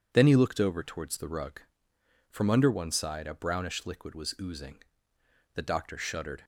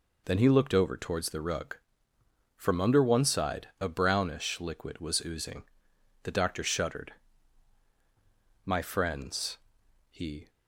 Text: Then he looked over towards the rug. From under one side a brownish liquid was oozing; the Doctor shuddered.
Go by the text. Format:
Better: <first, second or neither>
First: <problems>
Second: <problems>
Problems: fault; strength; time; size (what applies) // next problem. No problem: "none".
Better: first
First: none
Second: goes on to say "My friends he"; strong; from 8.6 s on; 1.8 s long